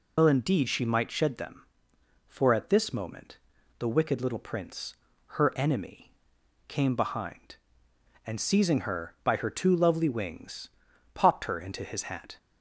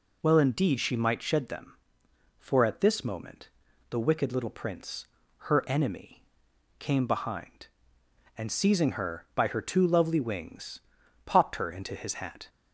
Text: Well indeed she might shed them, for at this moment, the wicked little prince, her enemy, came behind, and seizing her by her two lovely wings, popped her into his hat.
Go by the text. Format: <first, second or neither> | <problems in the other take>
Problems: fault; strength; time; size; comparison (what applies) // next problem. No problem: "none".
second | loses the start of "Well"; at 0.1 s; 65 ms